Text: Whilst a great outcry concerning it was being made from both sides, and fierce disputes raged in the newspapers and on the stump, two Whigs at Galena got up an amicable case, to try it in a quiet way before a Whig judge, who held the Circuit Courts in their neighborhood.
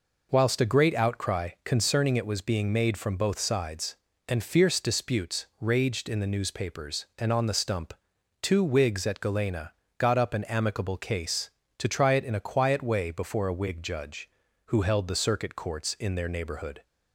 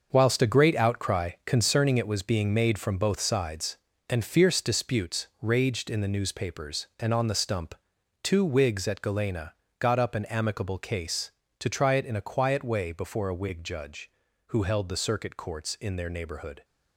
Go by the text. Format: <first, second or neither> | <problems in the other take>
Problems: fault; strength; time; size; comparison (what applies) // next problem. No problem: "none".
first | gets quieter; strong; throughout; 10 dB // pauses between "Galena" and "got"; slight; at 9.5 s; 0.24 s long; slight in the first